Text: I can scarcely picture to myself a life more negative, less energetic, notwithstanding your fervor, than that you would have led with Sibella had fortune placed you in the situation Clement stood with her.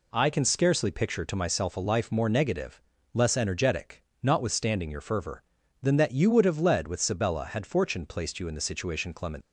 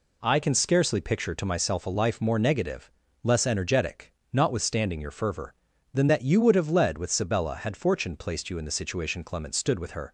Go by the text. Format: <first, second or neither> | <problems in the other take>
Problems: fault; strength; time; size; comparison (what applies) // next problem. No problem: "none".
second | stops before "stood with her"; at 9.4 s